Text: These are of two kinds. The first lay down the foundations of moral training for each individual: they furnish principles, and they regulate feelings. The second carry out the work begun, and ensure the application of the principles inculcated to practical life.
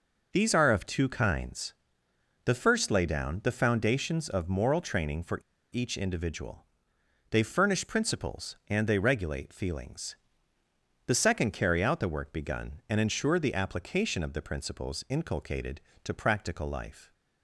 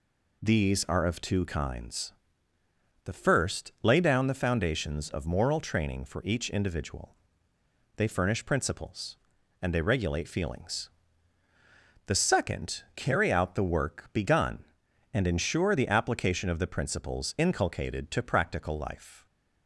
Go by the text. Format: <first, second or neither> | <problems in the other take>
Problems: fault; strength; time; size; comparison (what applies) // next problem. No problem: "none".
second | pauses between "for" and "each"; slight; at 5.4 s; 0.32 s long